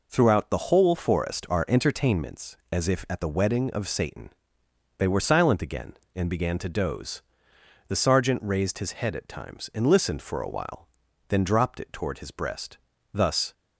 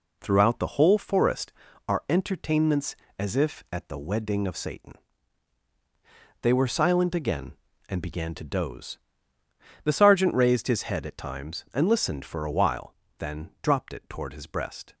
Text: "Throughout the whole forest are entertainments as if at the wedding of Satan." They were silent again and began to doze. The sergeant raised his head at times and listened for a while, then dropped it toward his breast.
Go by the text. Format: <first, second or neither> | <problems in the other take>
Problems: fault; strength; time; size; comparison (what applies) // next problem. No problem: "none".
second | goes on to say "Thus"; slight; from 13.1 s on; 0.40 s long